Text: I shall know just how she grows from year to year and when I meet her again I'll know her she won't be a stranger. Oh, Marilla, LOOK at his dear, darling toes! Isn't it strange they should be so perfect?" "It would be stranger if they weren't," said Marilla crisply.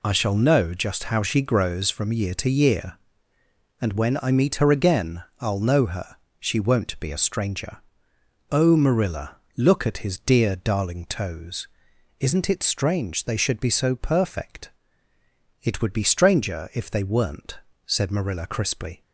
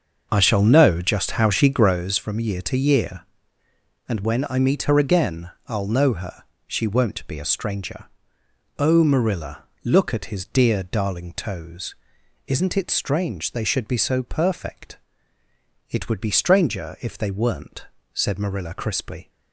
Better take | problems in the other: first | starts louder than the rest; until 2.0 s; 6.5 dB // pauses between "again" and "I'll"; slight; at 5.5 s; 0.16 s long; slight in the first // pauses between "her" and "she"; slight; at 6.4 s; 0.24 s long; slight in the first

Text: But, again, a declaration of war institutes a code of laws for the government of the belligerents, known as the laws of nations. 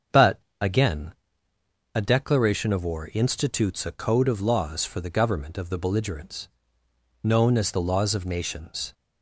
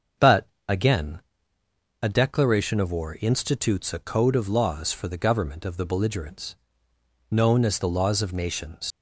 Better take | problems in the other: first | starts louder than the rest; until 2.1 s; 7 dB; also in the first // leaves "nations" unfinished; at 8.9 s; 105 ms

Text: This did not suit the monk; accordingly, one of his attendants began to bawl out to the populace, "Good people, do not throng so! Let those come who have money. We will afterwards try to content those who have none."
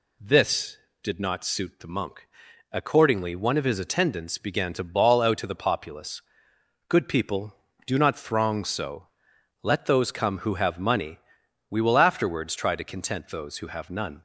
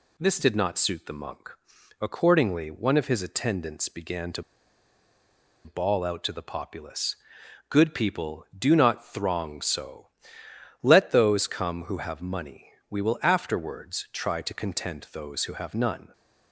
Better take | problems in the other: first | pauses between "to" and "bawl"; at 4.4 s; 1.2 s long

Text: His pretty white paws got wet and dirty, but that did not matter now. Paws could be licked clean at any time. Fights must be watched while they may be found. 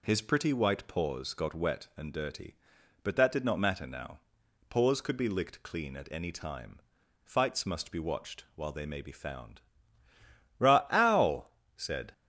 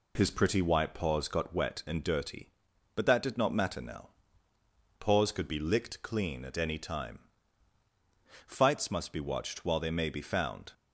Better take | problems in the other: second | goes on to say "Ra ow said"; from 10.5 s on; 1.5 s long

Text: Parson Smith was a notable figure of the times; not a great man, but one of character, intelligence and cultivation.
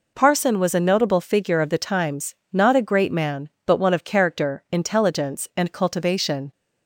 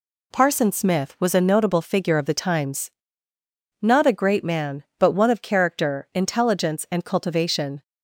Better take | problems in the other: second | skips "Smith"; at 0.5 s

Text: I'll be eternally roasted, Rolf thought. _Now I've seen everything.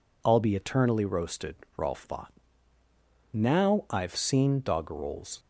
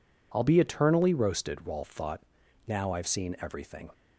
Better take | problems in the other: second | says "doggerels" for "everything"; at 4.6 s

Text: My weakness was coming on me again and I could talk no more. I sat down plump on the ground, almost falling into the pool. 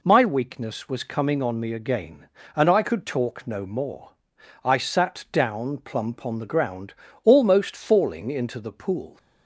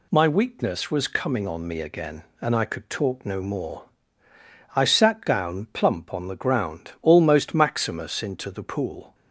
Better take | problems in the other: first | says "maximus" for "falling"; at 7.5 s

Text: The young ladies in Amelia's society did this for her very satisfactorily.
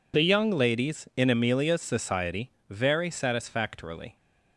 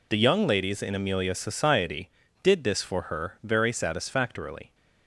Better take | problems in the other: second | skips "did this for her"; at 2.5 s

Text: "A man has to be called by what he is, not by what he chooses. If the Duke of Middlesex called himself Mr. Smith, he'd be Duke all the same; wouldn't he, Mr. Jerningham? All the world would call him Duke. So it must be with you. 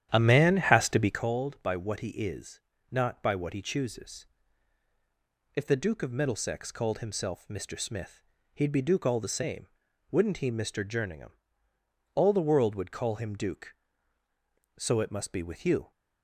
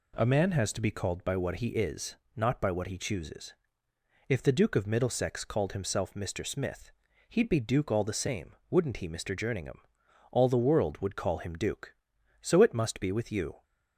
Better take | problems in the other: second | starts louder than the rest; strong; until 1.3 s; 10.5 dB

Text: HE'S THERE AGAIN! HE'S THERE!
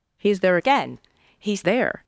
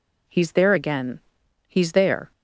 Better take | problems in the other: second | changes voice from "AGAIN" to "HE'S"; from 0.5 to 1.6 s; 1.1 s long

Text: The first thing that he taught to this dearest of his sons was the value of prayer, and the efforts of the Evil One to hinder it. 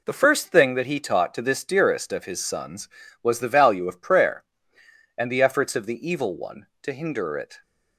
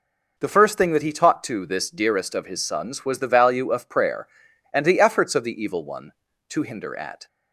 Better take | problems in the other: first | says "at" for "it"; at 6.9 s

